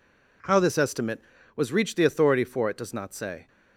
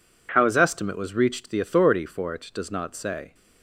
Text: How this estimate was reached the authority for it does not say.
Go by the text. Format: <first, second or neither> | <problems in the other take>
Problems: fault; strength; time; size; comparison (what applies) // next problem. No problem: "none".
first | says "his" for "this"; at 0.4 s